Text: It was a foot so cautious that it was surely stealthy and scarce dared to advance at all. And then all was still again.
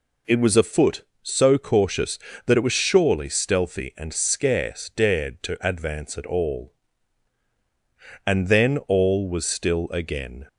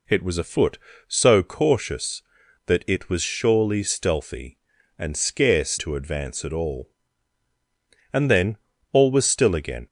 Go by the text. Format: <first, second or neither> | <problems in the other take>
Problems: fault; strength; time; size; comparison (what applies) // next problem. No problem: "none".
first | skips "dared"; at 5.7 s // pauses between "then" and "all"; slight; at 8.5 s; 0.36 s long